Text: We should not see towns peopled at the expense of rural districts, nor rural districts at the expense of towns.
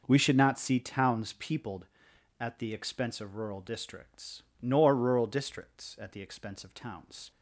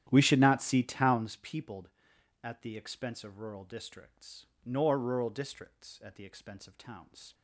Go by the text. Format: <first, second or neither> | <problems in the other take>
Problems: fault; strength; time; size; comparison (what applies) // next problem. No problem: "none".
first | starts louder than the rest; strong; until 1.4 s; 11 dB